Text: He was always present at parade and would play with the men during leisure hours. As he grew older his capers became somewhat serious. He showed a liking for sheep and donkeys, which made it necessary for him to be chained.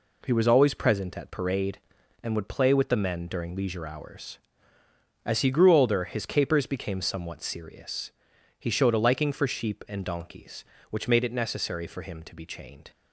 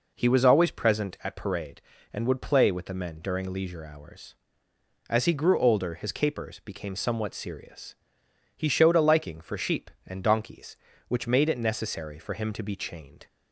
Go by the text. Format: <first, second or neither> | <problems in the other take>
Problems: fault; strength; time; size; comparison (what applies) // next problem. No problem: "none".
neither | none